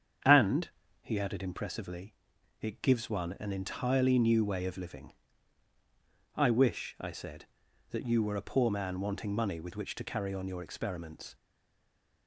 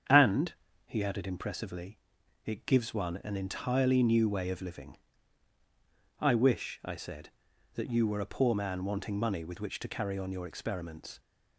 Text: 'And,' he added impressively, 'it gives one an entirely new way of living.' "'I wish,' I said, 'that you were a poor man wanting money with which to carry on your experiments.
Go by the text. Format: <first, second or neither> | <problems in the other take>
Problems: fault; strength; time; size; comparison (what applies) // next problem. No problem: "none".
second | starts louder than the rest; strong; until 1.5 s; 8 dB; strong in the second // stays silent after the last word; slight; from 11.3 s on; 0.9 s long